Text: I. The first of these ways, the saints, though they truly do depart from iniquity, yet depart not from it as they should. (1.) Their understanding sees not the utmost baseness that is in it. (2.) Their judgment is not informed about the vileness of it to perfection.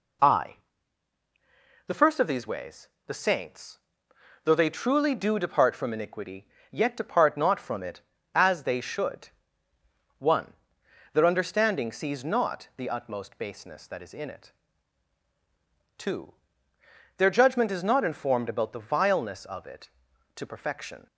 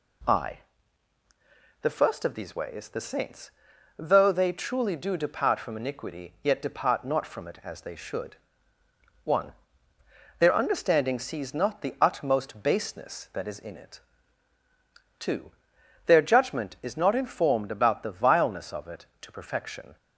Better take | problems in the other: neither | none

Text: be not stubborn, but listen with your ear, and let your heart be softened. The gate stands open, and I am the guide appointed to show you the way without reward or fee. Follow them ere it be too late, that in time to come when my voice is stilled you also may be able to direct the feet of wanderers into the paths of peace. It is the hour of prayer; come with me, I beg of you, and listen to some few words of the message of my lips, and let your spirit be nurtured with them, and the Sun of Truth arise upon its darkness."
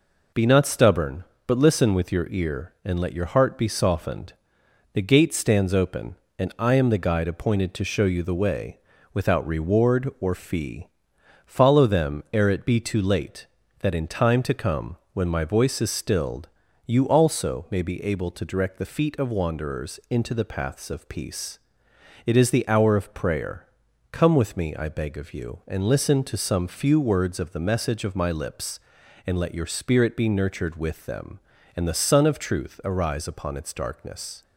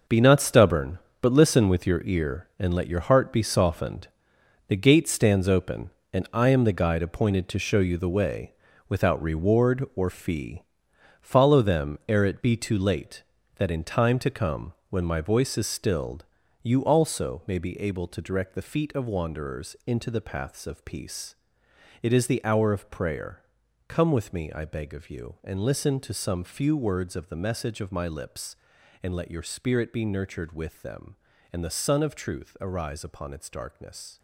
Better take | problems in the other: first | gets quieter; strong; throughout; 11 dB // pauses between "way" and "without"; slight; at 8.5 s; 0.36 s long; slight in the first // pauses between "come" and "when"; slight; at 14.7 s; 0.16 s long; slight in the first // pauses between "stilled" and "you"; slight; at 16.2 s; 0.36 s long; slight in the first

